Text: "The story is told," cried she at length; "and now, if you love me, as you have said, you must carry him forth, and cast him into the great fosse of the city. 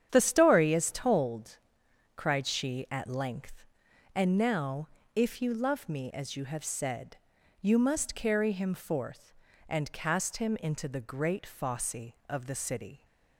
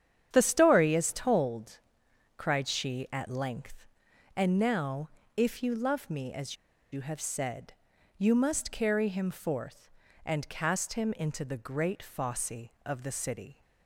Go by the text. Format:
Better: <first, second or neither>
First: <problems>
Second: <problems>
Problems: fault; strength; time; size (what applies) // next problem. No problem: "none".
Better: first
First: starts louder than the rest; strong; until 1.1 s; 9 dB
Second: starts louder than the rest; strong; until 1.3 s; 9 dB // pauses between "as" and "you"; at 6.5 s; 0.37 s long